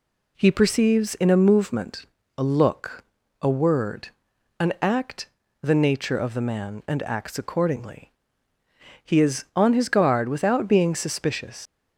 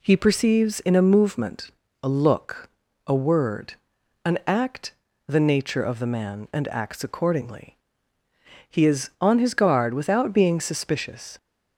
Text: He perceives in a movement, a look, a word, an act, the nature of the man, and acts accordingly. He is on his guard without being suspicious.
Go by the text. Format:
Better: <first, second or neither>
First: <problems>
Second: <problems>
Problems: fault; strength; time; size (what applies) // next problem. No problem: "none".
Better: second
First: leaves "suspicious" unfinished; at 11.6 s; 65 ms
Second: none